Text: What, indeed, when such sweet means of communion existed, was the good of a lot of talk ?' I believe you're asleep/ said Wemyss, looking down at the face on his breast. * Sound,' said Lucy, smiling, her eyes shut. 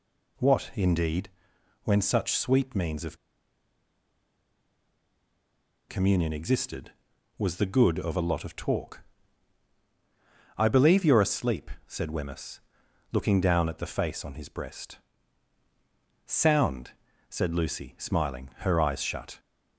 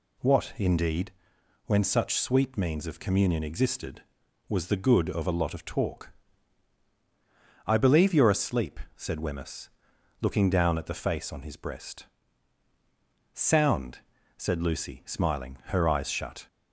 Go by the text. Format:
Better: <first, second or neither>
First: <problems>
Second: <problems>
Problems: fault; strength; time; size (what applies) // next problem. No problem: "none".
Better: second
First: pauses between "of" and "communion"; strong; at 3.1 s; 2.7 s long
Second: none